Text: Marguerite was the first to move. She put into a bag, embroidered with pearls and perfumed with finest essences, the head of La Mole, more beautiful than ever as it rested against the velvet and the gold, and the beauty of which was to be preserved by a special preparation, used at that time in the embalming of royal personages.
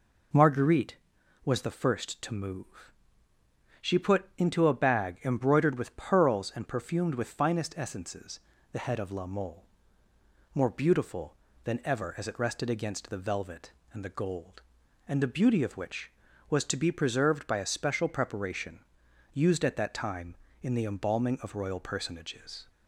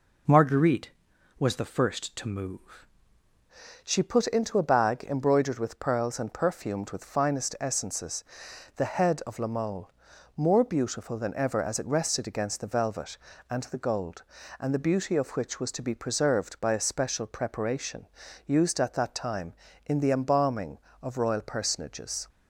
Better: first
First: none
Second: changes voice at "She"; from 3.8 s on; 18.4 s long

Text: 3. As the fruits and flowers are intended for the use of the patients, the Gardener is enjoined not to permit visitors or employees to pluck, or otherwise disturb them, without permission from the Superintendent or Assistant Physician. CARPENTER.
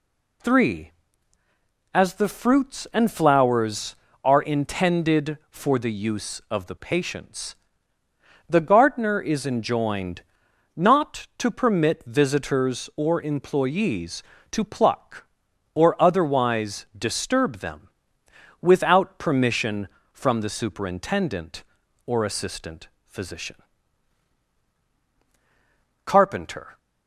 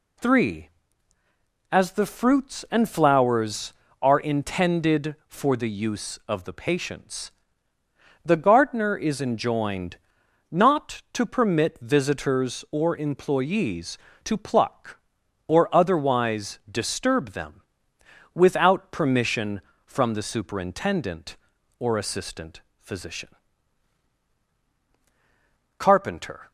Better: neither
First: pauses between "enjoined" and "not"; noticeable; at 10.2 s; 0.54 s long // pauses between "Assistant" and "Physician"; slight; at 22.8 s; 0.18 s long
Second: pauses between "enjoined" and "not"; noticeable; at 9.9 s; 0.54 s long // pauses between "Assistant" and "Physician"; slight; at 22.6 s; 0.18 s long

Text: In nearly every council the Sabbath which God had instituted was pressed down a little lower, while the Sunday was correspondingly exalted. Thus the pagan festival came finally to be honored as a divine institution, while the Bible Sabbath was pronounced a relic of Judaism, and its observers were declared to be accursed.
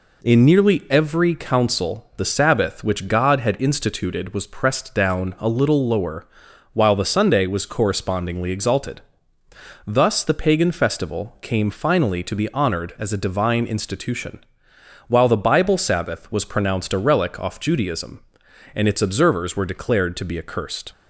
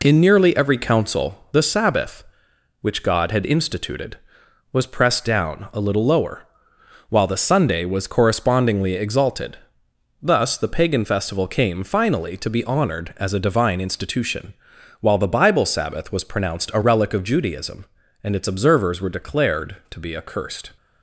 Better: second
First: says "off" for "of"; at 17.3 s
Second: none

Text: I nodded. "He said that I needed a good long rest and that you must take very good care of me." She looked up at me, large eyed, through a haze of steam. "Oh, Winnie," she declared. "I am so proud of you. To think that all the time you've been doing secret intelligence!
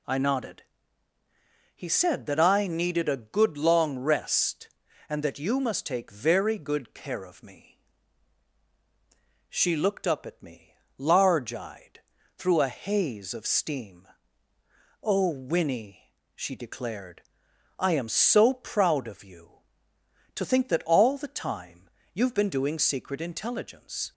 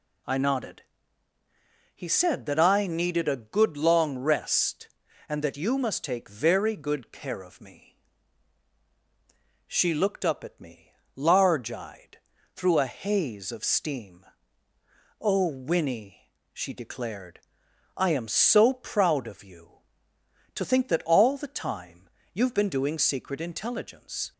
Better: neither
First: pauses between "time" and "you've"; slight; at 21.8 s; 0.26 s long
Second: pauses between "time" and "you've"; slight; at 22.0 s; 0.26 s long

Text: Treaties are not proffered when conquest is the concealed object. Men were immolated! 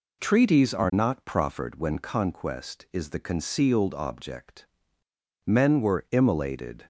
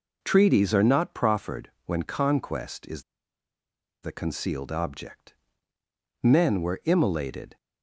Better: first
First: none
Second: pauses between "proffered" and "when"; slight; at 1.7 s; 0.16 s long // pauses between "is" and "the"; at 3.0 s; 0.99 s long

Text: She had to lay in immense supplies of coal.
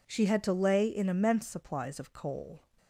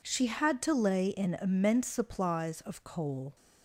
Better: neither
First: none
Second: none

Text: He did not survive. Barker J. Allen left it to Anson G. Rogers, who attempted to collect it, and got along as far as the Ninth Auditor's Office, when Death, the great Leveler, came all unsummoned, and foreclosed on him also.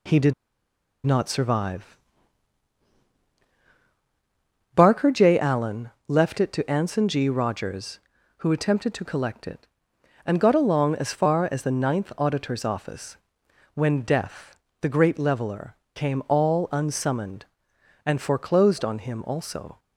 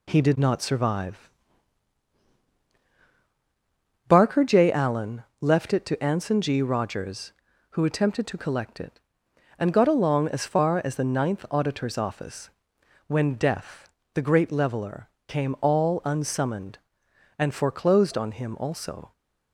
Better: second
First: pauses between "did" and "not"; noticeable; at 0.3 s; 0.73 s long // pauses between "Allen" and "left"; slight; at 5.8 s; 0.18 s long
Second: pauses between "Allen" and "left"; slight; at 5.2 s; 0.18 s long

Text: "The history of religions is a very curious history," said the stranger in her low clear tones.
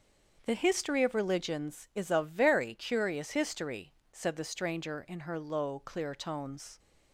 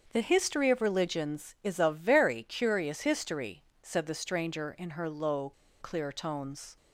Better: first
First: starts louder than the rest; until 1.4 s; 7 dB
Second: starts louder than the rest; until 1.1 s; 7 dB // pauses between "low" and "clear"; slight; at 5.5 s; 0.33 s long

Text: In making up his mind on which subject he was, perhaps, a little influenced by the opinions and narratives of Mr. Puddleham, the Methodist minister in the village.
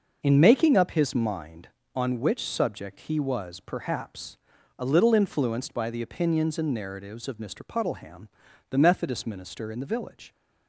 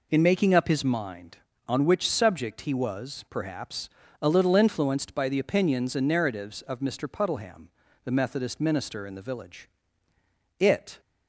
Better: first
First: none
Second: goes on to say "It"; slight; from 10.5 s on; 0.42 s long

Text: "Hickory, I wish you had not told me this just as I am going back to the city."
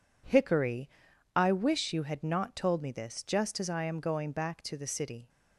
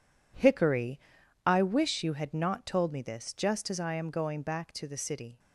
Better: first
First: none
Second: gets quieter; strong; throughout; 11.5 dB

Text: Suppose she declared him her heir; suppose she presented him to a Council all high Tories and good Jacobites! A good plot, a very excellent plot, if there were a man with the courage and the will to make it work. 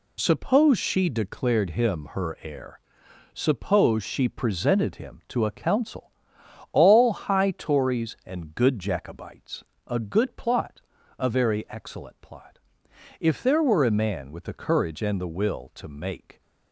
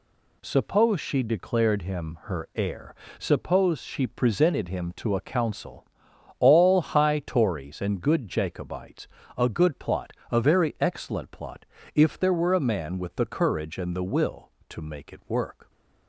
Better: second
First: pauses between "Council" and "all"; noticeable; at 6.1 s; 0.62 s long // stops before "it work"; at 16.4 s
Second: pauses between "Council" and "all"; noticeable; at 5.8 s; 0.56 s long

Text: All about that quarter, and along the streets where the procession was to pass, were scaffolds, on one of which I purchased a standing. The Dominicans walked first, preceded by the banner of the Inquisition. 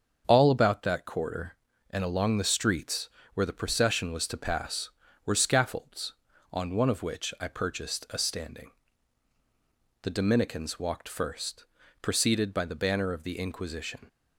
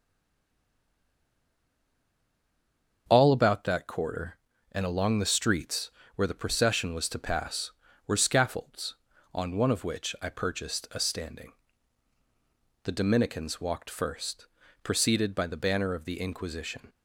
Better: first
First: starts louder than the rest; until 1.2 s; 7 dB // pauses between "streets" and "where"; slight; at 3.0 s; 0.26 s long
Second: stays silent before the first word; strong; until 3.0 s; 3.0 s long // starts louder than the rest; until 4.0 s; 7 dB // pauses between "streets" and "where"; slight; at 5.9 s; 0.26 s long

